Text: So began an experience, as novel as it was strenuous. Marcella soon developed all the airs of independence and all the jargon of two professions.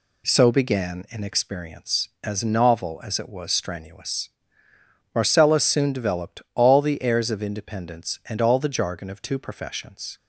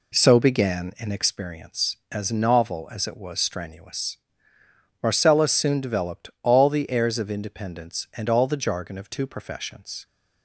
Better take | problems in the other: first | starts louder than the rest; slight; until 1.4 s; 2.5 dB

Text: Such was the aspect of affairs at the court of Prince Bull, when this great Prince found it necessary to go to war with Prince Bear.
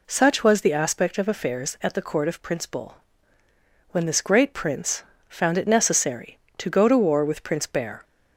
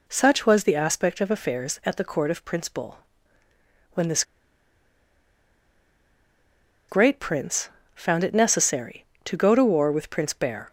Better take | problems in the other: first | pauses between "this" and "great"; strong; at 4.2 s; 2.6 s long // pauses between "Prince" and "found"; slight; at 7.6 s; 0.28 s long; slight in the first

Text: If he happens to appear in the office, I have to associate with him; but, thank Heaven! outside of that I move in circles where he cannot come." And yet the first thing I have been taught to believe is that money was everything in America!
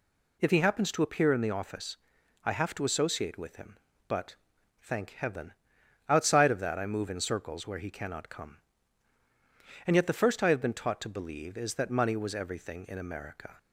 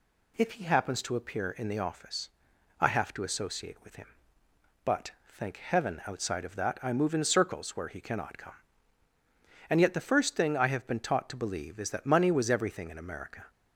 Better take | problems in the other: second | skips "thing"; at 10.4 s

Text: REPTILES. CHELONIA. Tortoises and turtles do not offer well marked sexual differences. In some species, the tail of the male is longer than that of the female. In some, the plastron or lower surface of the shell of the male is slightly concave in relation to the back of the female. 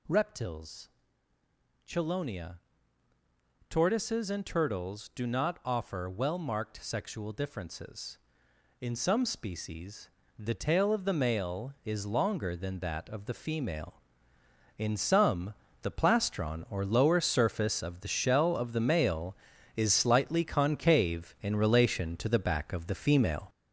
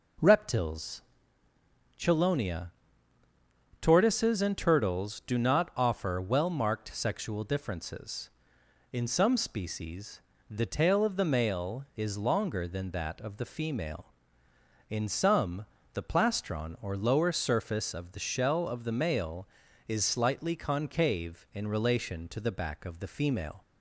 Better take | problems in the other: second | gets louder; throughout; 7 dB

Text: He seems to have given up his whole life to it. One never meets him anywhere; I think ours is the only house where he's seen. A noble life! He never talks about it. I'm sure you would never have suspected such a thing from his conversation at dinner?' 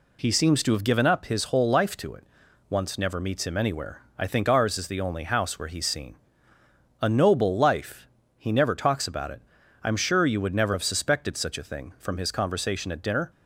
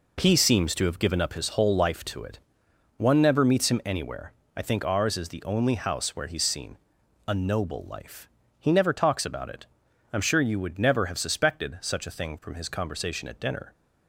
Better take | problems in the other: second | says "Once" for "One"; at 2.6 s

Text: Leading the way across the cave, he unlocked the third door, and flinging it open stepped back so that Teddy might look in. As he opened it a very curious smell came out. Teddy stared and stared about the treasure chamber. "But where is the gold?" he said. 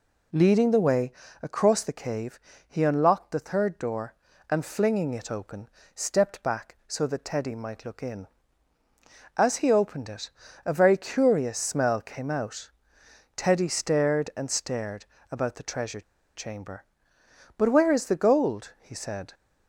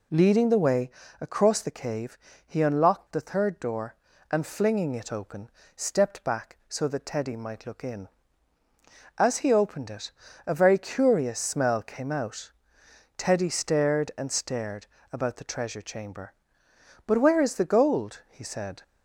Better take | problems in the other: second | pauses between "way" and "across"; slight; at 1.1 s; 0.30 s long; slight in the second // pauses between "open" and "stepped"; slight; at 5.6 s; 0.26 s long; slight in the second // pauses between "it" and "a"; slight; at 10.3 s; 0.34 s long; slight in the second // pauses between "stared" and "about"; slight; at 15.0 s; 0.26 s long; slight in the second // pauses between "treasure" and "chamber"; slight; at 16.0 s; 0.34 s long

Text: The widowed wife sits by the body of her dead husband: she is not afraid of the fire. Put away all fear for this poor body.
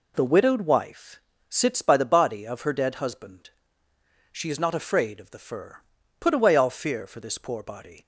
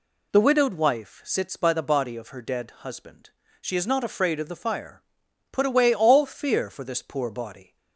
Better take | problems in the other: second | pauses between "wife" and "sits"; slight; at 1.1 s; 0.30 s long // says "fur" for "fire"; at 5.3 s

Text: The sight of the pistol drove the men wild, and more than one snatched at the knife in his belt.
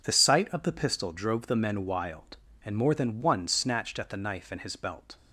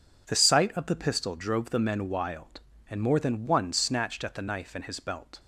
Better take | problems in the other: neither | none

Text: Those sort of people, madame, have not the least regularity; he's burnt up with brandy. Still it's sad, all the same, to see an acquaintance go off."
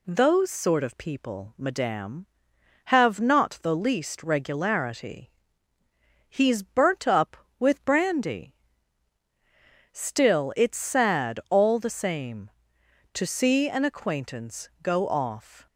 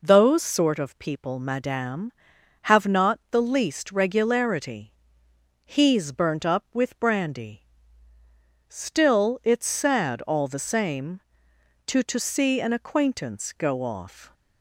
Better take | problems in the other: first | says "to" twice; at 12.0 s

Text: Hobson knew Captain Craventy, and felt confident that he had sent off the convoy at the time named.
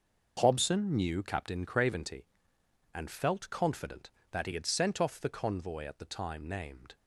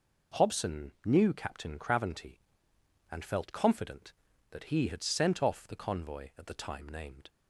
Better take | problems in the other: neither | none

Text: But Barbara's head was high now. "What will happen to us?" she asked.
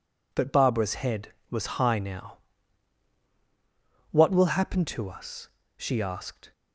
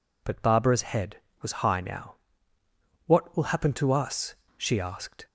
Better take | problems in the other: neither | none

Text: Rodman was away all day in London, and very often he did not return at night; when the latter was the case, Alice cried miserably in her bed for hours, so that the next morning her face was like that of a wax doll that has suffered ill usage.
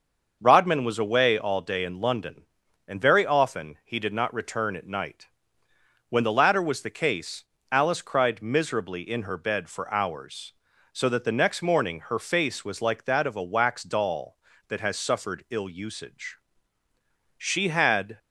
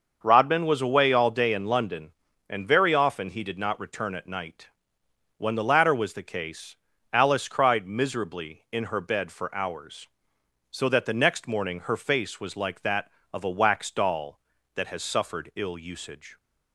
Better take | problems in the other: second | starts louder than the rest; until 1.4 s; 6 dB; also in the second // goes on to say "She had"; noticeable; from 17.3 s on; 0.80 s long

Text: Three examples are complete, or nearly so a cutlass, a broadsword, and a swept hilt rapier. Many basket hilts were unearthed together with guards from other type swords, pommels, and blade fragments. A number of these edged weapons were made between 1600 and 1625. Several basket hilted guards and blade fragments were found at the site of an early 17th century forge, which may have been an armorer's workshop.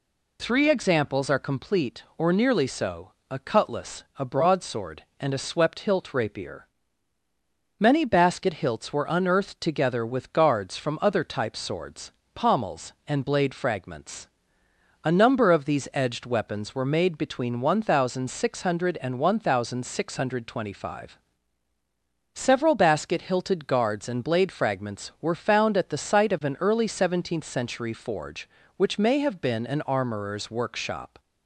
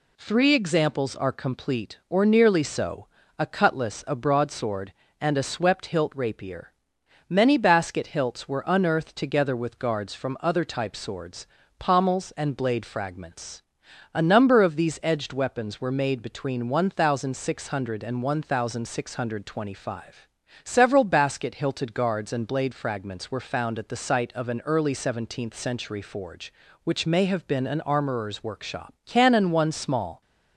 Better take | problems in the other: first | pauses between "so" and "a"; slight; at 3.0 s; 0.30 s long; slight in the first // goes on to say "CANNON One small"; noticeable; from 29.0 s on; 1.1 s long

